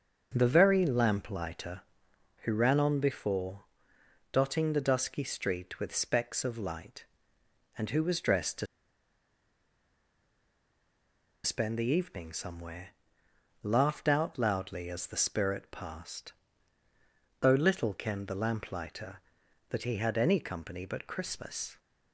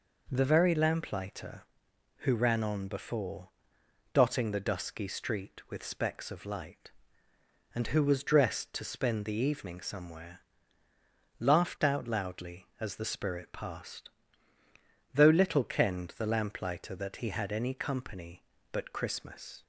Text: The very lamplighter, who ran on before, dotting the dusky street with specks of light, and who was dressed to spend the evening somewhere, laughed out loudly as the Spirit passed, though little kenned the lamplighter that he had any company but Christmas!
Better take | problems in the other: second | starts louder than the rest; until 1.3 s; 6.5 dB // pauses between "to" and "spend"; strong; at 8.6 s; 2.7 s long

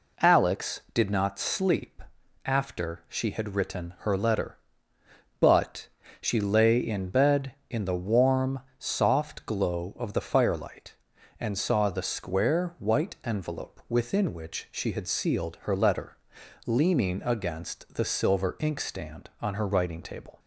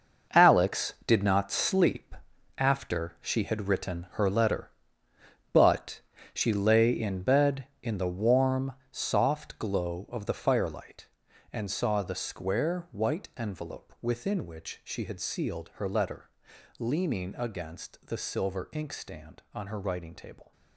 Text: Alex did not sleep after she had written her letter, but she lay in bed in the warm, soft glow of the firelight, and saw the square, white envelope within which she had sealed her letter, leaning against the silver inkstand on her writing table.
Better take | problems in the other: first | gets quieter; strong; throughout; 12 dB // pauses between "sleep" and "after"; at 2.1 s; 0.44 s long; also in the first // pauses between "but" and "she"; slight; at 6.0 s; 0.32 s long; slight in the first

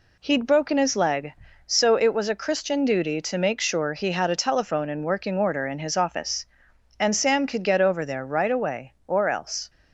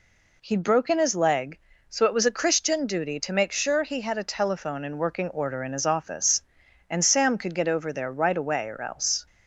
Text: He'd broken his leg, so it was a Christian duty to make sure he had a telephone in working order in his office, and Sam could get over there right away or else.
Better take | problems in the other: neither | none

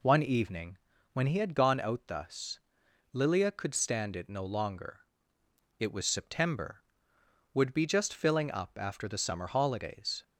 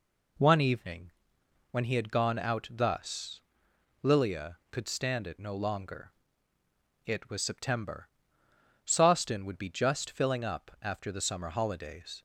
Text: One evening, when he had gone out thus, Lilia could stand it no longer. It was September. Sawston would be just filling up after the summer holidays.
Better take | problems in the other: second | skips "Sawston"; at 7.1 s

